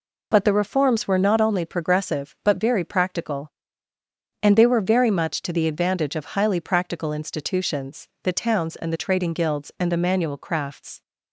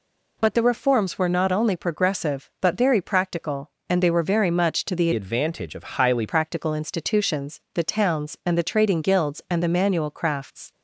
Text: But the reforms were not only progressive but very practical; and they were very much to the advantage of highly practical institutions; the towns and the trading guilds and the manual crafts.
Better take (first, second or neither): first